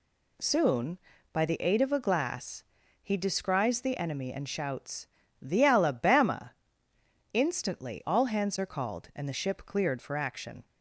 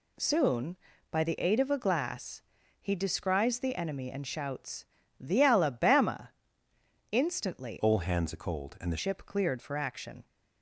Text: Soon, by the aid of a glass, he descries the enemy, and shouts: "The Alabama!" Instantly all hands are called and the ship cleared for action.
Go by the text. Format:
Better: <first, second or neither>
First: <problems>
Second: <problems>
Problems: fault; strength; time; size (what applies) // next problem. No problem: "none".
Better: first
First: none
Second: changes voice from "all" to "the"; from 7.7 to 8.9 s; 1.2 s long